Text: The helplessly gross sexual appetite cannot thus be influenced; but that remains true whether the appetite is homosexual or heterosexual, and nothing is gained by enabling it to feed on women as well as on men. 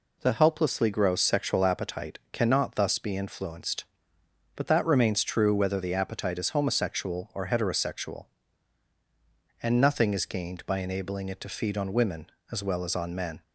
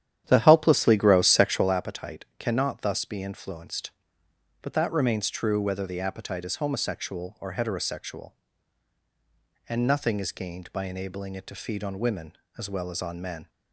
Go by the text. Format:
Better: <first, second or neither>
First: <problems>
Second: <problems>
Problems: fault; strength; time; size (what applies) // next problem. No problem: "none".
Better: first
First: none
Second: starts louder than the rest; strong; until 1.7 s; 10.5 dB